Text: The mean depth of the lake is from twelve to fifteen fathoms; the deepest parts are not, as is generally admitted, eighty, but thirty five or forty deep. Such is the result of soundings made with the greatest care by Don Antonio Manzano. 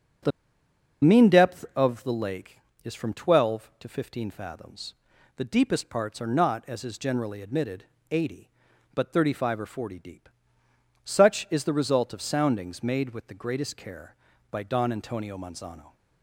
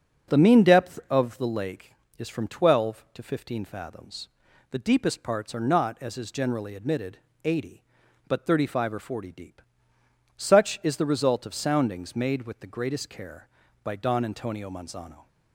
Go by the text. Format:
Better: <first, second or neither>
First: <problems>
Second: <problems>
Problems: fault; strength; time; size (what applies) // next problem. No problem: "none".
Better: second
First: starts louder than the rest; until 2.0 s; 6.5 dB // pauses between "The" and "mean"; noticeable; at 0.3 s; 0.72 s long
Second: starts louder than the rest; until 1.3 s; 6.5 dB